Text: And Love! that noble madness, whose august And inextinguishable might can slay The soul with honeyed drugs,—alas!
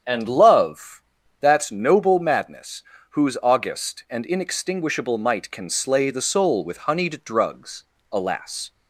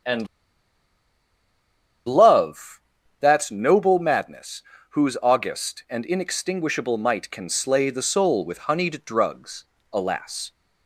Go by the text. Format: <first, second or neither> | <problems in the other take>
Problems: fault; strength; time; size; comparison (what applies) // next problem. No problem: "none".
first | starts louder than the rest; strong; until 3.2 s; 7.5 dB; strong in the first // pauses between "And" and "Love"; strong; at 0.2 s; 1.7 s long